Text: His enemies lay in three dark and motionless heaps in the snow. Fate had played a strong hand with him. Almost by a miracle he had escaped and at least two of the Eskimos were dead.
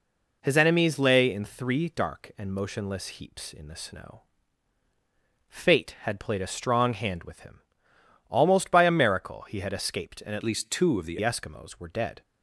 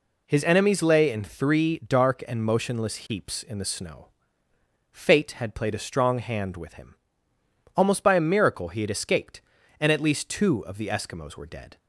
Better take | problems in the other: second | changes voice from "least" to "the"; from 10.4 to 11.1 s; 0.7 s long

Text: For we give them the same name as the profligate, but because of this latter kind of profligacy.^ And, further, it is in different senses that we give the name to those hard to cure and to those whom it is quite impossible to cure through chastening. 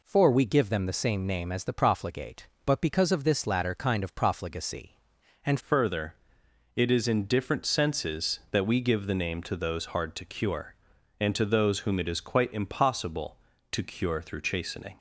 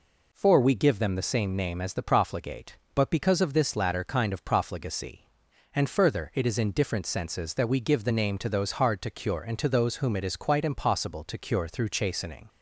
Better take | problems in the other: second | changes voice at "further"; from 5.5 s on; 9.4 s long

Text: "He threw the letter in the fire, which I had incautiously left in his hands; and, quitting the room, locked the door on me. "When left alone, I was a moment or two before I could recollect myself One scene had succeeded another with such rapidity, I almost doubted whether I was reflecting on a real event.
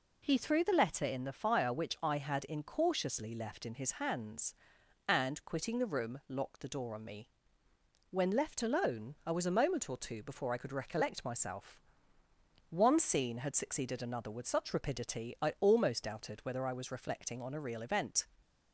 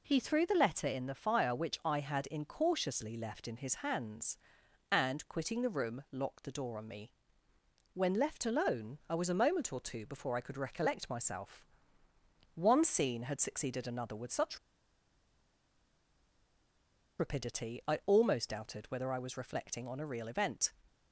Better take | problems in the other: first | pauses between "myself" and "One"; noticeable; at 11.6 s; 0.88 s long; noticeable in the first // pauses between "such" and "rapidity"; strong; at 14.5 s; 2.6 s long

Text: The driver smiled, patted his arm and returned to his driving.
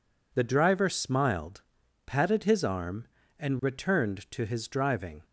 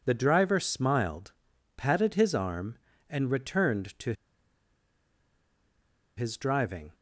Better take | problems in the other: first | pauses between "to" and "his"; strong; at 4.1 s; 2.0 s long

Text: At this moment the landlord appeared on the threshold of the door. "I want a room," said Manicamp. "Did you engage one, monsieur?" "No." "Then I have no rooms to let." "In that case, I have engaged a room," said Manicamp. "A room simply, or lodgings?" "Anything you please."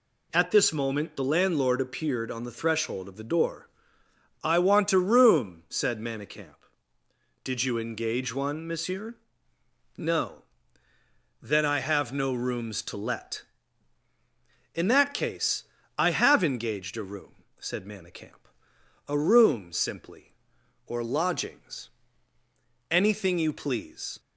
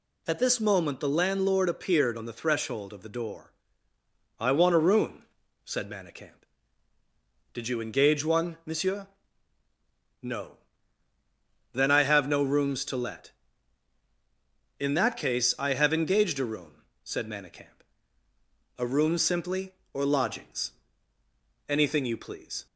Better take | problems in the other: neither | none

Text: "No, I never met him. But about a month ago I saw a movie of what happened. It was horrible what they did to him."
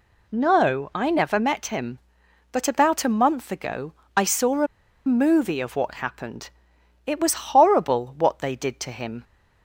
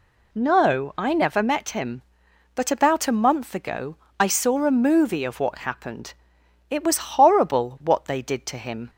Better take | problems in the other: second | pauses between "ago" and "I"; slight; at 3.9 s; 0.20 s long; slight in the second // pauses between "a" and "movie"; at 4.6 s; 0.40 s long

